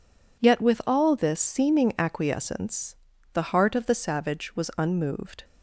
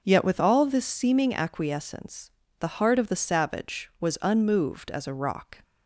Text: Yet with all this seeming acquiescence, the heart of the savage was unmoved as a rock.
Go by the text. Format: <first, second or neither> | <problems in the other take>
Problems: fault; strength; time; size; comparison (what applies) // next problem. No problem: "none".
second | stops before "as a rock"; at 5.4 s